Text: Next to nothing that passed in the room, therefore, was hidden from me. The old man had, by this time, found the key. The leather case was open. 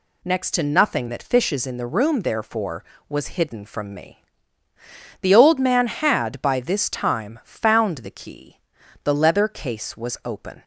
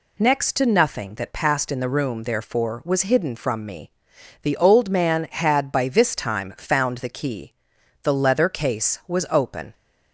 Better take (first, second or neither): second